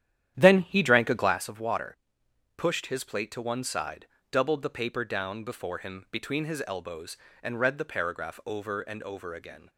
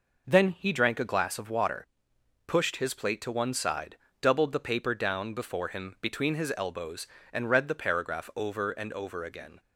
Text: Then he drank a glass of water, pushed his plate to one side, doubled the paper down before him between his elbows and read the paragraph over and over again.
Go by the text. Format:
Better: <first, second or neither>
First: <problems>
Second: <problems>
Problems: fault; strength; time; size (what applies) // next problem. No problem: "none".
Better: second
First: starts louder than the rest; strong; until 1.5 s; 11 dB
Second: none